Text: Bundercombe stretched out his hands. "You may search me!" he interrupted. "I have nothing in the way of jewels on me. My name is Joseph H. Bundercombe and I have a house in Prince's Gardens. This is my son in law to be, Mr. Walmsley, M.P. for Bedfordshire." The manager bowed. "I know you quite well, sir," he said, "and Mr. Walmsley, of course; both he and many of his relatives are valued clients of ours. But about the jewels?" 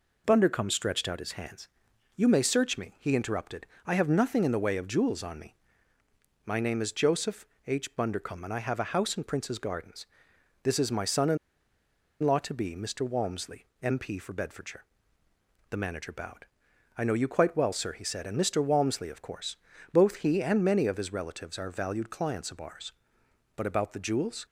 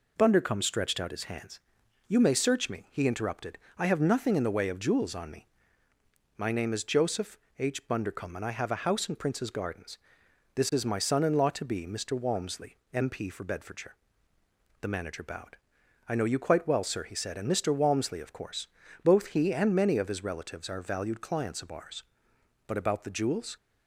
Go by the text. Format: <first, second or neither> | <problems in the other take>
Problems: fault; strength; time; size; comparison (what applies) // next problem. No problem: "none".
second | pauses between "Joseph" and "H"; slight; at 7.4 s; 0.20 s long; slight in the second // pauses between "in" and "law"; noticeable; at 11.3 s; 0.85 s long